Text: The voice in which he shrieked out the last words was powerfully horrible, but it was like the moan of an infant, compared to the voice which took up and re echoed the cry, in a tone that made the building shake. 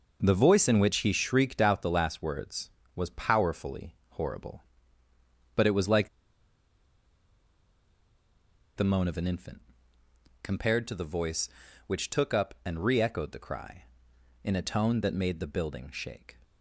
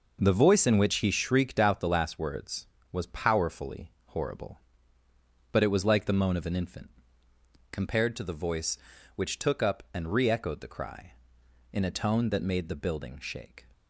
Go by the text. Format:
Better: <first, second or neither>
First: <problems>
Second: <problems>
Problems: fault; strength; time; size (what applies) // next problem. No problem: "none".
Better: second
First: pauses between "like" and "the"; strong; at 6.0 s; 2.6 s long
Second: none